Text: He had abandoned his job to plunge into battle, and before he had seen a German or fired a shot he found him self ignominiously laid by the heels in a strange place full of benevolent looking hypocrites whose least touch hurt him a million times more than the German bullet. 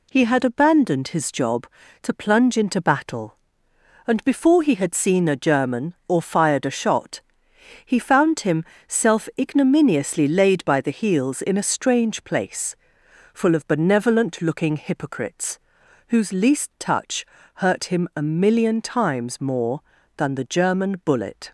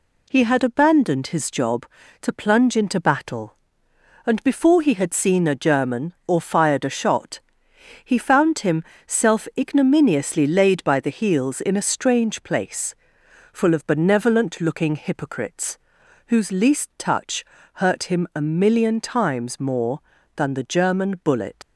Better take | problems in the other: first | pauses between "shot" and "he"; noticeable; at 7.4 s; 0.64 s long; noticeable in the first // pauses between "him" and "self"; slight; at 8.8 s; 0.24 s long; slight in the first // pauses between "place" and "full"; noticeable; at 12.9 s; 0.58 s long; noticeable in the first // pauses between "hypocrites" and "whose"; noticeable; at 15.7 s; 0.48 s long; noticeable in the first // pauses between "touch" and "hurt"; slight; at 17.4 s; 0.30 s long; slight in the first // leaves "bullet" unfinished; at 21.6 s; 85 ms

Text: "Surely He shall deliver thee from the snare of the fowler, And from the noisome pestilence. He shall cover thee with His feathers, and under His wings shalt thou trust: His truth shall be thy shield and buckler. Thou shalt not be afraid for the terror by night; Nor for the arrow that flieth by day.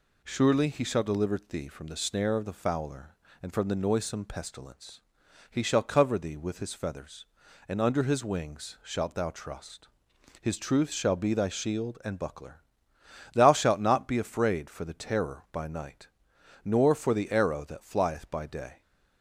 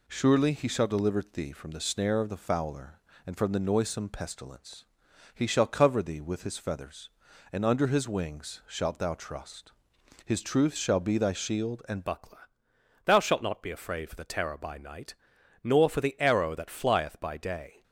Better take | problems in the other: first | changes voice at "buckler"; from 12.0 s on; 5.8 s long

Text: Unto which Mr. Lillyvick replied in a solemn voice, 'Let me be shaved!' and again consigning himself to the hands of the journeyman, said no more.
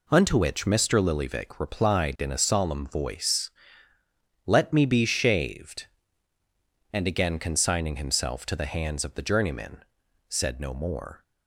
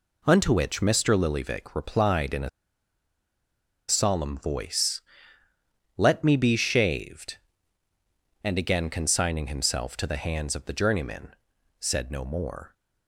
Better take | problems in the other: first | pauses between "a" and "solemn"; strong; at 2.4 s; 1.3 s long

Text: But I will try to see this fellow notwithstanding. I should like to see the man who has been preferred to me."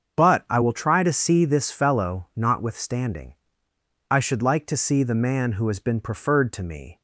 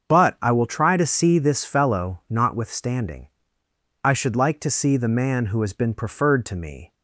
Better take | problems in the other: neither | starts louder than the rest; the same in both

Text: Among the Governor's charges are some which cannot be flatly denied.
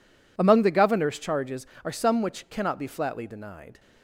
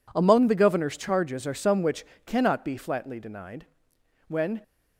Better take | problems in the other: first | pauses between "which" and "cannot"; slight; at 2.0 s; 0.20 s long // goes on to say "When"; slight; from 4.2 s on; 0.34 s long

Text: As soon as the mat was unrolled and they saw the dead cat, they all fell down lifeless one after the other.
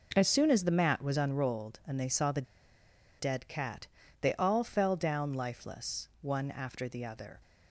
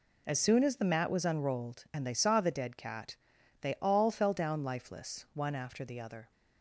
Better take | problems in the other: second | pauses between "the" and "dead"; noticeable; at 2.4 s; 0.77 s long

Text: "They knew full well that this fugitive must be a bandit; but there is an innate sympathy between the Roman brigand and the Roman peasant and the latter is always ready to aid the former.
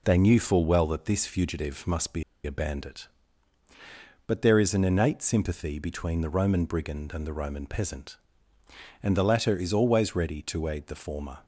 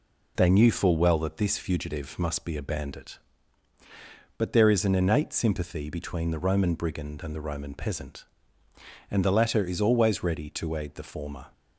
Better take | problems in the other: second | pauses between "be" and "a"; slight; at 2.2 s; 0.22 s long

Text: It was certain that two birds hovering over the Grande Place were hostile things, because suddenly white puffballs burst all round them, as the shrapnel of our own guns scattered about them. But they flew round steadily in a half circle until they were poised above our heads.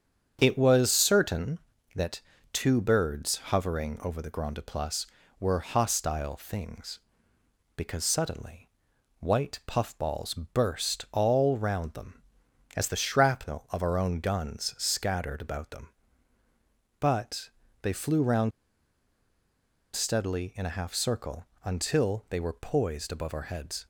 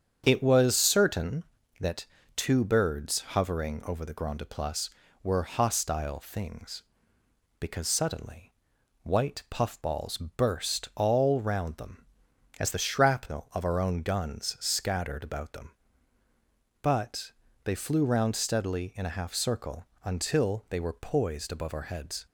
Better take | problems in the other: second | starts louder than the rest; strong; until 1.4 s; 8 dB; strong in the second // pauses between "that" and "two"; slight; at 2.2 s; 0.32 s long; slight in the second // pauses between "suddenly" and "white"; noticeable; at 8.6 s; 0.50 s long; noticeable in the second // pauses between "But" and "they"; slight; at 17.4 s; 0.32 s long; slight in the second // pauses between "round" and "steadily"; strong; at 18.5 s; 1.4 s long // pauses between "circle" and "until"; slight; at 21.4 s; 0.18 s long; slight in the second

